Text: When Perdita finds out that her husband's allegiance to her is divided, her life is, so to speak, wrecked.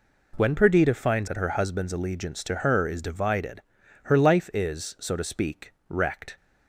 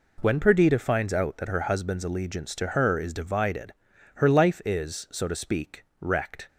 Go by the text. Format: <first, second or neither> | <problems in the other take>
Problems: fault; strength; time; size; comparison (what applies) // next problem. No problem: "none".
second | skips "out"; at 1.2 s